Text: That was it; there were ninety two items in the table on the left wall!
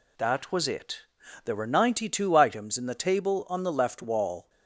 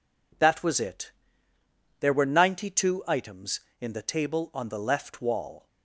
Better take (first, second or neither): neither